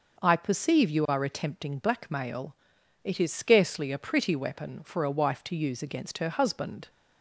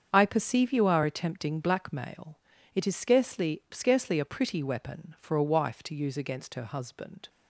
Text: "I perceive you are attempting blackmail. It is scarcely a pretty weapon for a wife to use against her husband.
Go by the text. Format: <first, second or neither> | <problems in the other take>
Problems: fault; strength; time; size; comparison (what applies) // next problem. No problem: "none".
first | starts louder than the rest; strong; until 1.1 s; 7.5 dB // says "scarcely" twice; at 3.7 s